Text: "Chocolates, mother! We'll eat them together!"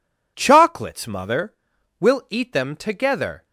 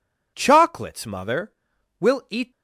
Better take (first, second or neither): first